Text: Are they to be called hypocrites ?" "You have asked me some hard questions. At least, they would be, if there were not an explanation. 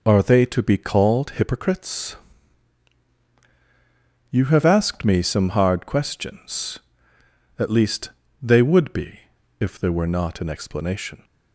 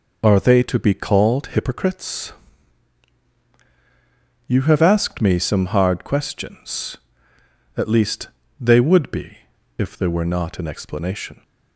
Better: neither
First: none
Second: none

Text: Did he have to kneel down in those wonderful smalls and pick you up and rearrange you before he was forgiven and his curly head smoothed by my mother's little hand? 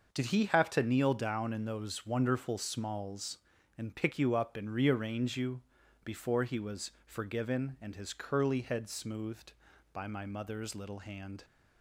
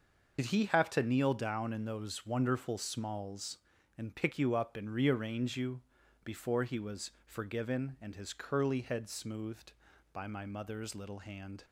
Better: first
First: starts louder than the rest; until 1.1 s; 6 dB // pauses between "you" and "before"; at 5.6 s; 0.42 s long // pauses between "was" and "forgiven"; slight; at 6.9 s; 0.16 s long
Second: loses the start of "Did"; at 0.3 s; 60 ms // starts louder than the rest; until 1.4 s; 6 dB // pauses between "you" and "before"; at 5.8 s; 0.42 s long // pauses between "was" and "forgiven"; slight; at 7.1 s; 0.16 s long

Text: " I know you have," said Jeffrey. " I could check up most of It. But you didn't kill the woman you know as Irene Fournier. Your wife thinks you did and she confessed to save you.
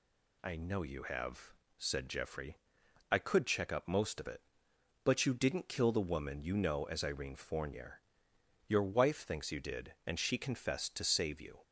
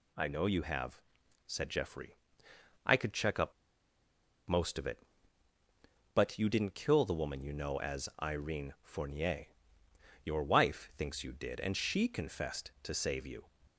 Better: first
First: none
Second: pauses between "up" and "most"; noticeable; at 3.5 s; 0.95 s long

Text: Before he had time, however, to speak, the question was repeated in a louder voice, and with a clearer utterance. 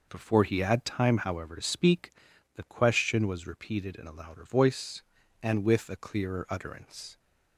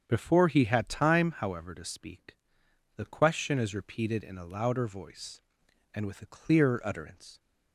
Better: first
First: none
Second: starts louder than the rest; strong; until 1.0 s; 7.5 dB // says "is" for "was"; at 3.5 s

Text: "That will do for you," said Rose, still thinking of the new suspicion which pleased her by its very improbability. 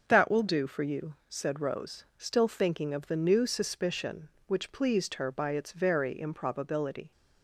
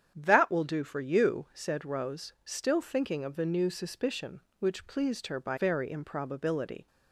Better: first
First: starts louder than the rest; until 1.0 s; 6.5 dB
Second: starts louder than the rest; strong; until 1.1 s; 8.5 dB // skips "its"; at 5.5 s

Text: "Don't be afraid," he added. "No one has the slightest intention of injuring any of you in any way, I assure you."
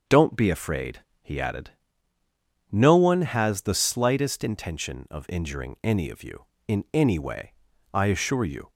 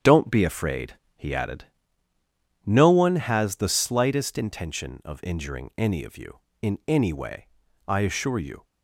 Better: first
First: starts louder than the rest; until 1.2 s; 6.5 dB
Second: gets quieter; throughout; 7 dB // starts louder than the rest; strong; until 1.2 s; 8.5 dB

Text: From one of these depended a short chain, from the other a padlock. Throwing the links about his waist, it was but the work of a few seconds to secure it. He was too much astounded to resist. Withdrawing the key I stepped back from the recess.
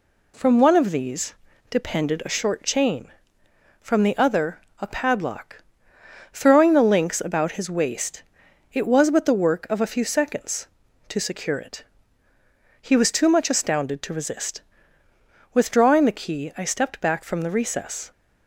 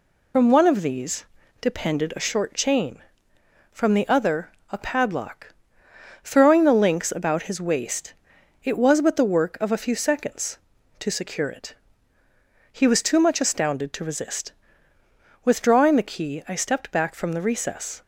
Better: first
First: pauses between "these" and "depended"; at 1.3 s; 0.38 s long // pauses between "other" and "a"; slight; at 4.5 s; 0.22 s long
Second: loses the start of "From"; at 0.3 s; 90 ms // pauses between "these" and "depended"; at 1.2 s; 0.38 s long // pauses between "other" and "a"; slight; at 4.4 s; 0.22 s long

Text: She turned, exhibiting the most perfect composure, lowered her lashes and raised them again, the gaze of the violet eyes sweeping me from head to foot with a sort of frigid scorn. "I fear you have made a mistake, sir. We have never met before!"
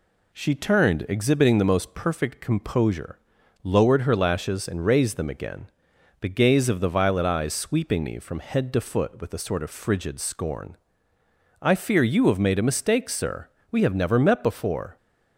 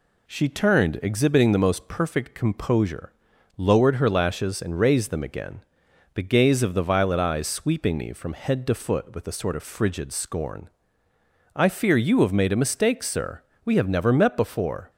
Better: neither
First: none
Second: none

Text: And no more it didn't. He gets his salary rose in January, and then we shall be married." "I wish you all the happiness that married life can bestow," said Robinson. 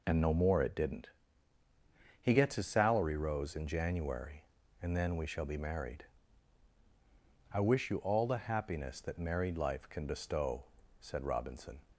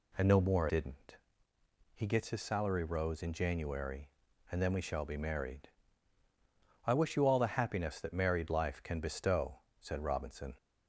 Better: first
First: none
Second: skips "it"; at 0.6 s

